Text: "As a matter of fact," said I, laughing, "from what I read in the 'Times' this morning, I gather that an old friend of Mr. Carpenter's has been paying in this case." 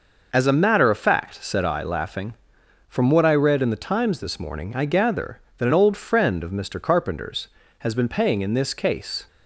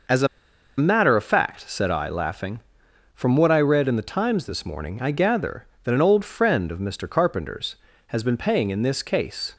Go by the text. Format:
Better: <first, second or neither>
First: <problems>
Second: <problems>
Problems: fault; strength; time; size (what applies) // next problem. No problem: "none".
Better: first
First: none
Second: pauses between "a" and "matter"; noticeable; at 0.2 s; 0.50 s long